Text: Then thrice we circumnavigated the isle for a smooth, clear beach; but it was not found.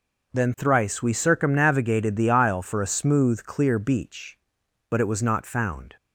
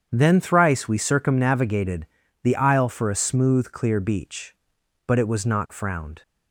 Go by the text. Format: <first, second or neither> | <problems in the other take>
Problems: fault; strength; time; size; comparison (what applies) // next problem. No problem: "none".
first | starts louder than the rest; strong; until 1.1 s; 7.5 dB // pauses between "circumnavigated" and "the"; slight; at 2.0 s; 0.36 s long // says "frowned" for "found"; at 5.7 s